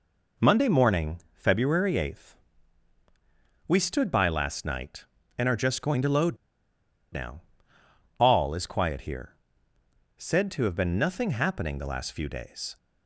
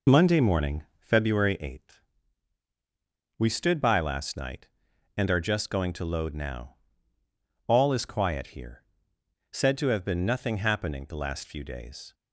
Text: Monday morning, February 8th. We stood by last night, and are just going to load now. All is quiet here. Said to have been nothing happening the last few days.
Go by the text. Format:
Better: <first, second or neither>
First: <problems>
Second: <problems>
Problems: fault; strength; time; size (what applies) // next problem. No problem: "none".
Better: second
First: pauses between "load" and "now"; noticeable; at 6.3 s; 0.76 s long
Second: none